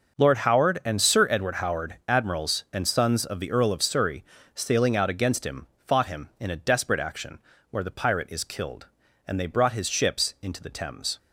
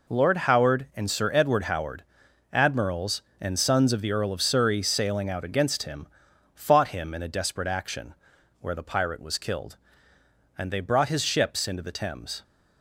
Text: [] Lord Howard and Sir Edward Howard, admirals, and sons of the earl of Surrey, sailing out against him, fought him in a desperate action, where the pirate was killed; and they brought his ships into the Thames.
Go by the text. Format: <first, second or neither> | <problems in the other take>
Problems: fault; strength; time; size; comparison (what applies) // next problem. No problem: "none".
second | says "is" for "was"; at 8.2 s